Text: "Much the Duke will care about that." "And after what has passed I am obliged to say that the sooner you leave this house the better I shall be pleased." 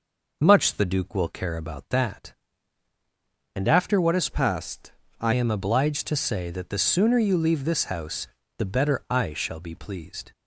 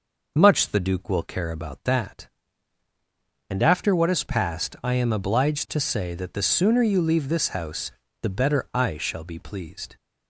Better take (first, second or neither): second